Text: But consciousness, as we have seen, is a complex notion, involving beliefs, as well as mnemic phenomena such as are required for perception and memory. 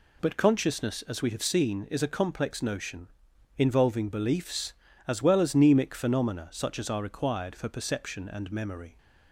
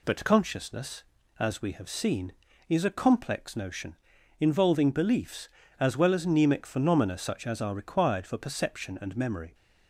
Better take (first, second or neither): neither